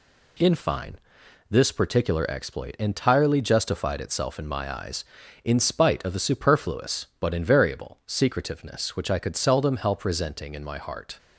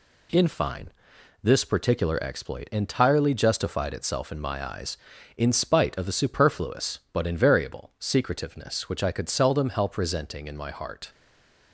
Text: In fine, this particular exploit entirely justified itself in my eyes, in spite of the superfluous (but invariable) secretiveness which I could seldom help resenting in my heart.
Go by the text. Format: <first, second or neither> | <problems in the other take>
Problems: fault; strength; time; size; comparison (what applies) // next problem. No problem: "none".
first | stays silent after the last word; slight; from 11.1 s on; 0.6 s long